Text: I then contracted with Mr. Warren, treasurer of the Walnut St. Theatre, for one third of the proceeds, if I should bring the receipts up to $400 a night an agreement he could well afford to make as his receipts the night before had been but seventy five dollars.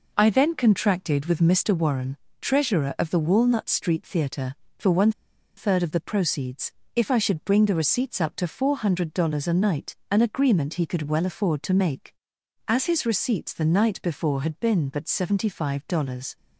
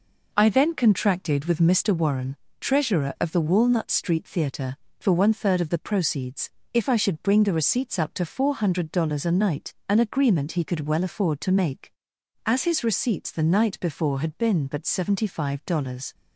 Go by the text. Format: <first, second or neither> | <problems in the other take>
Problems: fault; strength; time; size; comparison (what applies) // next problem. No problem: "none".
second | pauses between "one" and "third"; noticeable; at 5.1 s; 0.46 s long